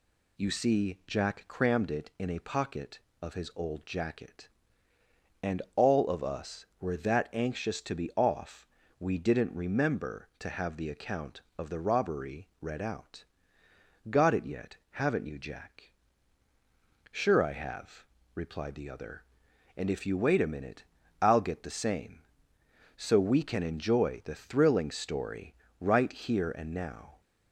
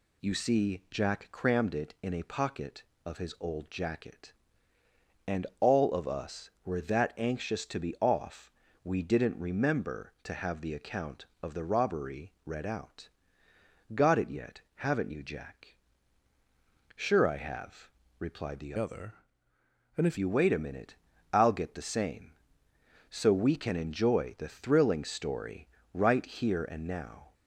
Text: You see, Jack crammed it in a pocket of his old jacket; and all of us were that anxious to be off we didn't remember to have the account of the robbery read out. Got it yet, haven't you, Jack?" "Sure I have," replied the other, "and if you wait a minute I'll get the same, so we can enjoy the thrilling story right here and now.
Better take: first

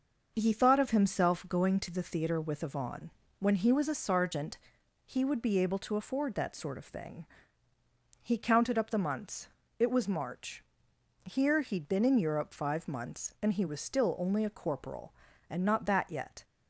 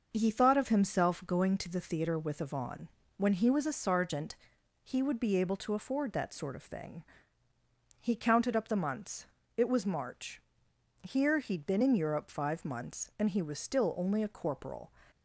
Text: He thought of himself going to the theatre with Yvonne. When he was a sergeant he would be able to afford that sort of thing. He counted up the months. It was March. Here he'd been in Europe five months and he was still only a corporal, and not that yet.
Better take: first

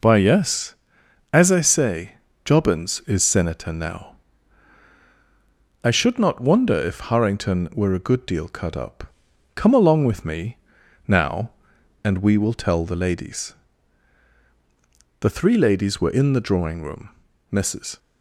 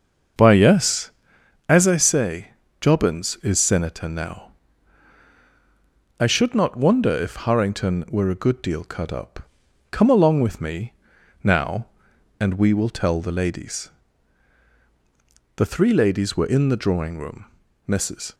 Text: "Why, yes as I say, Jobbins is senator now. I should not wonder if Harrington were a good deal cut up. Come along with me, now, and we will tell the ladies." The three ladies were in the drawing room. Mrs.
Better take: first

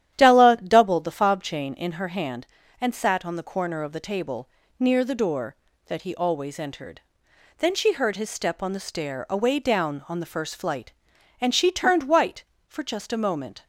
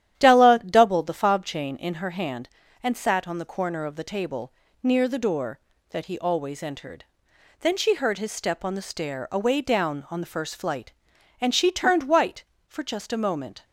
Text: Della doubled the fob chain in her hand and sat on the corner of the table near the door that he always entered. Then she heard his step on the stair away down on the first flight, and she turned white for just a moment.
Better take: neither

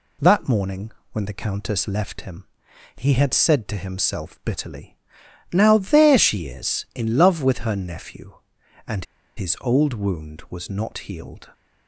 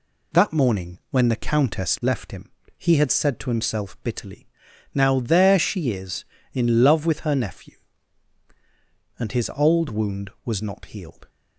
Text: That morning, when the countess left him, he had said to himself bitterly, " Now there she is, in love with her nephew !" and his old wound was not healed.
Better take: second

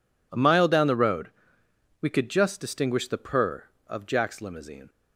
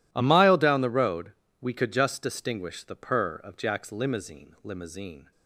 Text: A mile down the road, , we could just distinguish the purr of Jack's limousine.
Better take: first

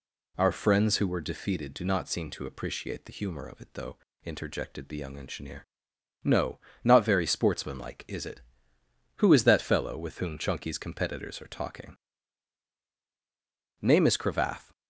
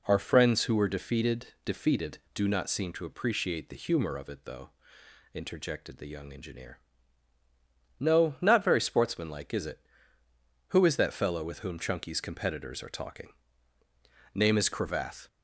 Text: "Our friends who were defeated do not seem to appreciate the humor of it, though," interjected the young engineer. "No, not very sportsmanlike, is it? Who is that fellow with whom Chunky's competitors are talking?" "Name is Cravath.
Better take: first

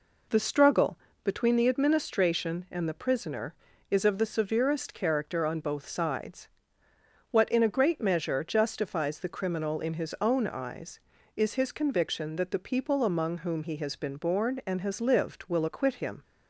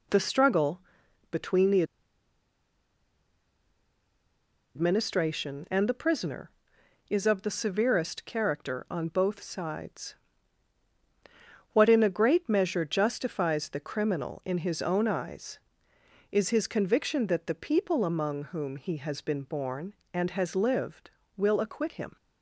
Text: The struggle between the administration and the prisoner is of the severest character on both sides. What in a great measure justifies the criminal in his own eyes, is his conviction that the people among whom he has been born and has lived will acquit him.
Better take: first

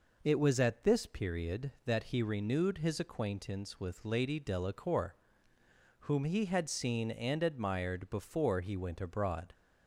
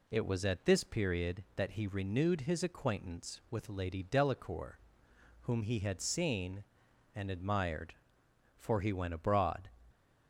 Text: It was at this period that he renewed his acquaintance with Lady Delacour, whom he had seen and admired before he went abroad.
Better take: first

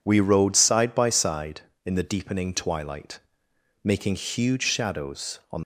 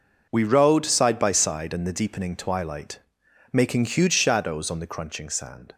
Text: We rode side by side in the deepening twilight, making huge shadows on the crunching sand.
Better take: second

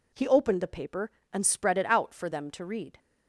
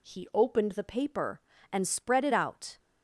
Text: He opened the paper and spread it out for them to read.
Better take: first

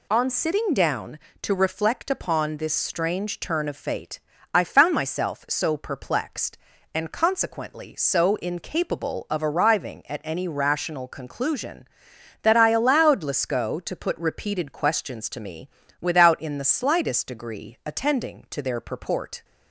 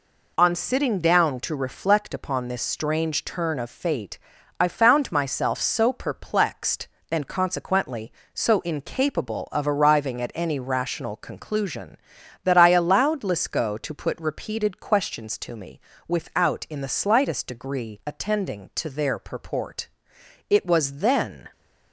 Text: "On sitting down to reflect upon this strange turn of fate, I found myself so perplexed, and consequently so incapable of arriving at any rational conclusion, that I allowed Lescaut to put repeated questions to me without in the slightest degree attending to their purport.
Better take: first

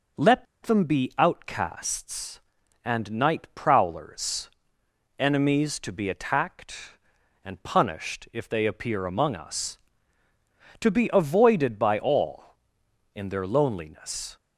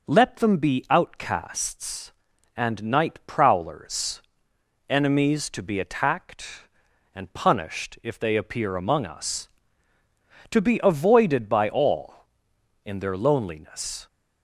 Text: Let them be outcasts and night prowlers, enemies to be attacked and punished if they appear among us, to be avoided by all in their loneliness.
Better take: second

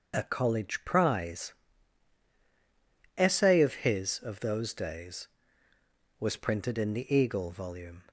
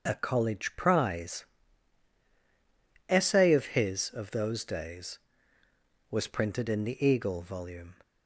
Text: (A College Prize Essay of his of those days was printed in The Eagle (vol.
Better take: neither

